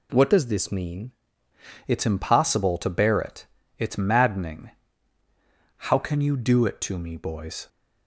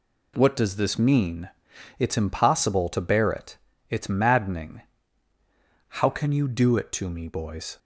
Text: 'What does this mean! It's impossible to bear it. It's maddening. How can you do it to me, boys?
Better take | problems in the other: second | changes voice from "does" to "mean"; from 0.2 to 1.0 s; 0.8 s long

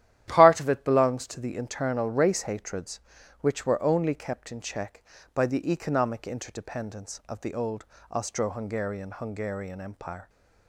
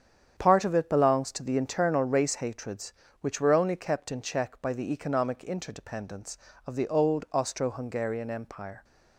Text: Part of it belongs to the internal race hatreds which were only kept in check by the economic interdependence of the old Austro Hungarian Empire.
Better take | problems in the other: second | starts louder than the rest; strong; until 1.2 s; 12 dB; strong in the second // pauses between "old" and "Austro"; slight; at 7.8 s; 0.24 s long // says "Hungarian" twice; at 9.1 s

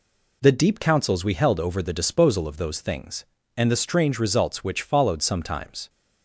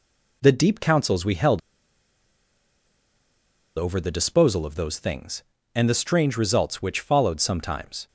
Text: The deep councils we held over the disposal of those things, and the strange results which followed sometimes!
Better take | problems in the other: first | pauses between "held" and "over"; strong; at 1.5 s; 2.1 s long

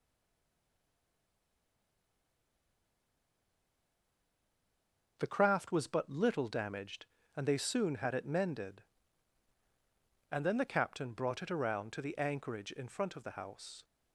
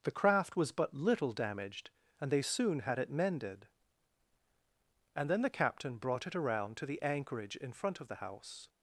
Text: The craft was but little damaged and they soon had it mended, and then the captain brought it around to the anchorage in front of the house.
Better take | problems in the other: second | stays silent before the first word; strong; until 5.1 s; 5.1 s long

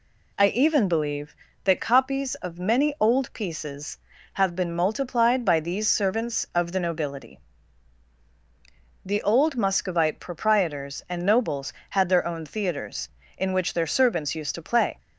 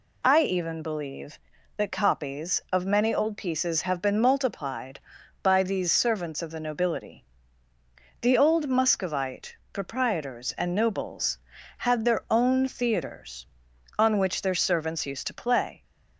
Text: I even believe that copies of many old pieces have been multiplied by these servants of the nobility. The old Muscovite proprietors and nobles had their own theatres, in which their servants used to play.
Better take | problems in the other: first | pauses between "Muscovite" and "proprietors"; slight; at 9.5 s; 0.16 s long // says "on" for "in"; at 13.9 s

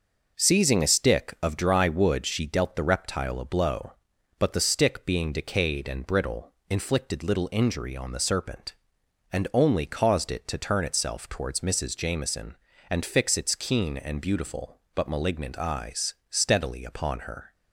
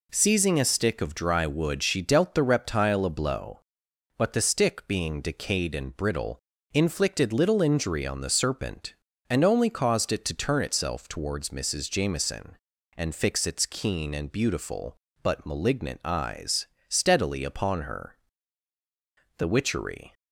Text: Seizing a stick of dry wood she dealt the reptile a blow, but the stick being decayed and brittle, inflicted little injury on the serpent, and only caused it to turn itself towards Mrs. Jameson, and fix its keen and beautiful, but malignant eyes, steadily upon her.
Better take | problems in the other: first | goes on to say "The witchery"; noticeable; from 19.3 s on; 0.76 s long

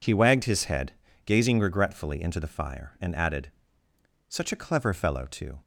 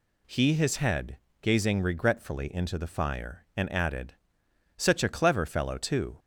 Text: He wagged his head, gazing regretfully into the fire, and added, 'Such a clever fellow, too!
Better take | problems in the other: first | skips "wagged"; at 0.5 s

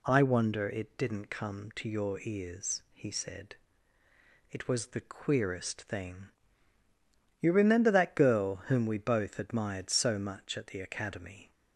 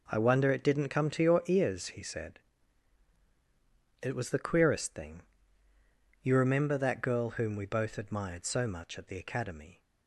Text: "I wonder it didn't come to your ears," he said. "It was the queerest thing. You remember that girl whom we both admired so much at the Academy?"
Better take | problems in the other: neither | none

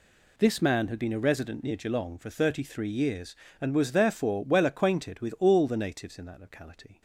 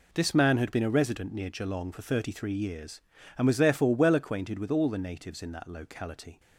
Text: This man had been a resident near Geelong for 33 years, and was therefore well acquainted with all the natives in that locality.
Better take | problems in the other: neither | none

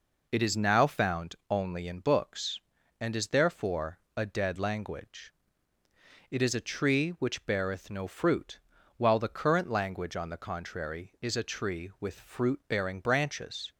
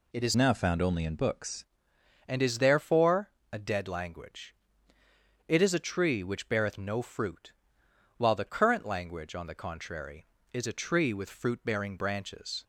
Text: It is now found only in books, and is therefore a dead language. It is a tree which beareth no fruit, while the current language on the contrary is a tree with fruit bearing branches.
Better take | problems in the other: first | changes voice from "now" to "books"; from 0.3 to 1.6 s; 1.3 s long // pauses between "therefore" and "a"; slight; at 3.3 s; 0.20 s long; slight in the first

